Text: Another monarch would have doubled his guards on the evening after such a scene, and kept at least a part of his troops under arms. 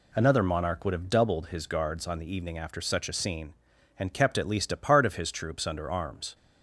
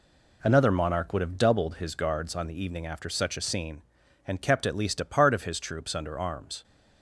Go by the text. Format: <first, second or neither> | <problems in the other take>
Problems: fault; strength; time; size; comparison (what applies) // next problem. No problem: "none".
first | gets quieter; throughout; 6.5 dB